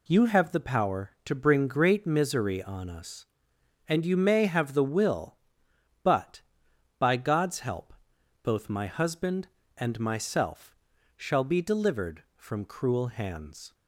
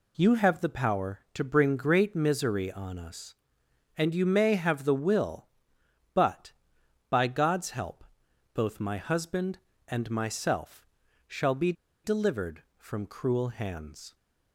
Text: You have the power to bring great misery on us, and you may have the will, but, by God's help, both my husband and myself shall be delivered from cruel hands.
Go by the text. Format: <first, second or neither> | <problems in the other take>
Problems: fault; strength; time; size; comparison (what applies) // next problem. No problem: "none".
first | pauses between "myself" and "shall"; at 10.8 s; 0.40 s long; also in the first // pauses between "be" and "delivered"; slight; at 11.7 s; 0.31 s long